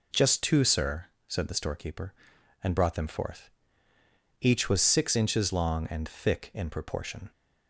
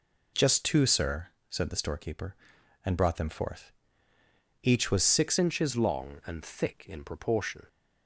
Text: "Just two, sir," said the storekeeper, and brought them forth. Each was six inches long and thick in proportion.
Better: first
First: none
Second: changes voice at "inches"; from 5.3 s on; 2.3 s long

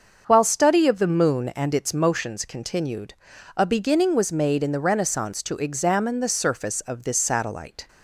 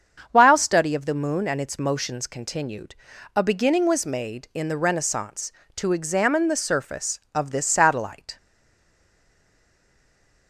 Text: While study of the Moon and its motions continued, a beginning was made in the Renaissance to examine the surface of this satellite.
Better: first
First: starts louder than the rest; until 1.3 s; 6.5 dB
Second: starts louder than the rest; strong; until 1.3 s; 7 dB // stays silent after the last word; from 8.3 s on; 2.1 s long

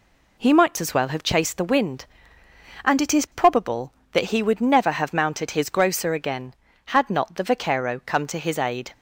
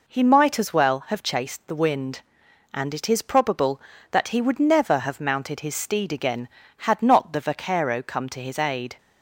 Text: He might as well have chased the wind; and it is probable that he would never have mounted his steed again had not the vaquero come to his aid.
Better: second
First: says "grocer" for "steed"; at 5.6 s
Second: none

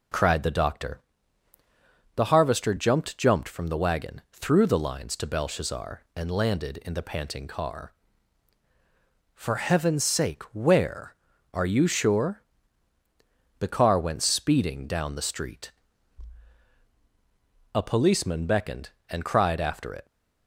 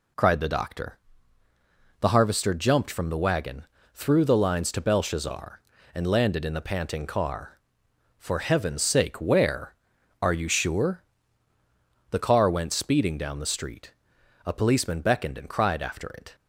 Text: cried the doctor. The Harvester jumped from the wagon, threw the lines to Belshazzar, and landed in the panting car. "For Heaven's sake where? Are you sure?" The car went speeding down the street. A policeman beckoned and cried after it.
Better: second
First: says "jumped" twice; at 3.1 s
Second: none

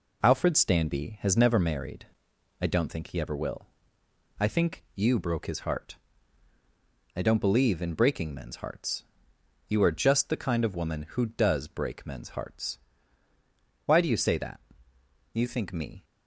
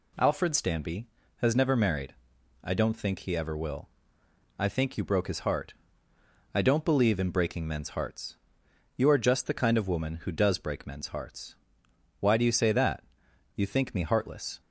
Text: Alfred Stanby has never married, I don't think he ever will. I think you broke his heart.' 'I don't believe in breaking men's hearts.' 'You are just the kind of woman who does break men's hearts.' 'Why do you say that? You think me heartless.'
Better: second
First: stops before "heartless"; at 16.0 s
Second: none

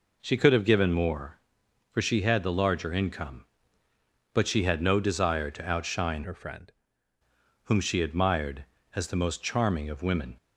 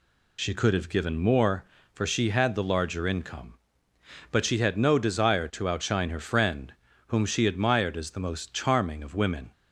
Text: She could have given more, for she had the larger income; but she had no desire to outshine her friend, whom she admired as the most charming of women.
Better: second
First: changes voice from "her" to "friend"; from 6.2 to 6.7 s; 0.5 s long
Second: none

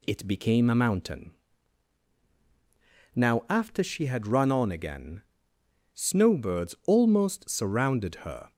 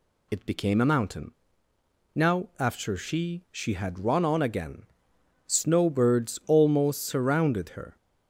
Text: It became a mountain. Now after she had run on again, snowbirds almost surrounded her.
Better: first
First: none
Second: says "she" twice; at 3.5 s

